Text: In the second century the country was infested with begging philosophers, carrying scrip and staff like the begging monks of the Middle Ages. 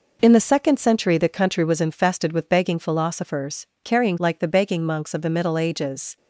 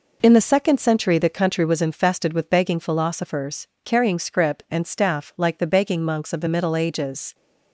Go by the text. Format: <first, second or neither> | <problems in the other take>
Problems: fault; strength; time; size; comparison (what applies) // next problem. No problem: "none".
second | skips "scrip and staff"; at 4.1 s